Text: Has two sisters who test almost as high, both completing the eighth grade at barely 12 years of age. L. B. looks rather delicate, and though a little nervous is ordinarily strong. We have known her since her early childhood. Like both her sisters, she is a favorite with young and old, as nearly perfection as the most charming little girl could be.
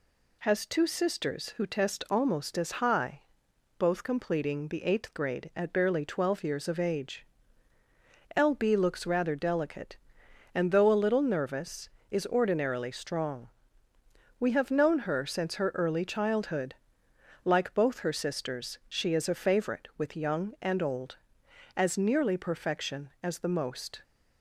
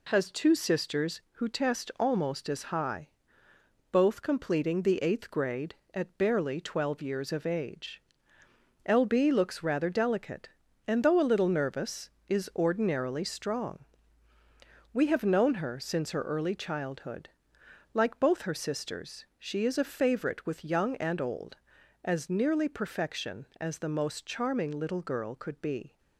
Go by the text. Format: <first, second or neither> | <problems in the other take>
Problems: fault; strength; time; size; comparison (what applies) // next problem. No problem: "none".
second | stops before "charming little girl could be"; at 24.0 s